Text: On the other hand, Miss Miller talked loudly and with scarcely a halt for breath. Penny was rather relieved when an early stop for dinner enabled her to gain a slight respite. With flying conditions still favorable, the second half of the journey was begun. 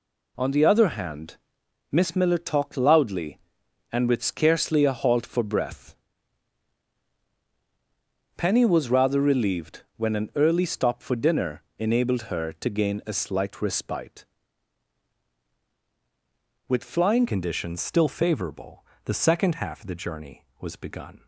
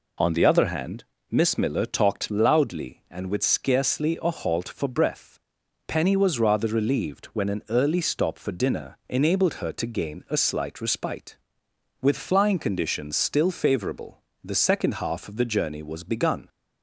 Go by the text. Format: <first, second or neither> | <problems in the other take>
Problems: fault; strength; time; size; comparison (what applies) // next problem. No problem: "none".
second | pauses between "dinner" and "enabled"; slight; at 11.6 s; 0.16 s long // changes voice at "conditions"; from 17.2 s on; 4.0 s long